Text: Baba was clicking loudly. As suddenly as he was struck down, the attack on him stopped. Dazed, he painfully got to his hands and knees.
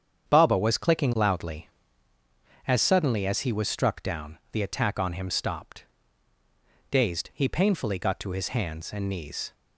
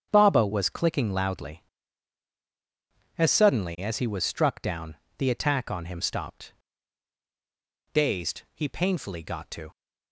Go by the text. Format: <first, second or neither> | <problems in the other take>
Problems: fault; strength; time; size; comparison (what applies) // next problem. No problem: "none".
first | starts louder than the rest; strong; until 1.1 s; 7.5 dB; strong in the first // stops before "his hands and knees"; at 9.7 s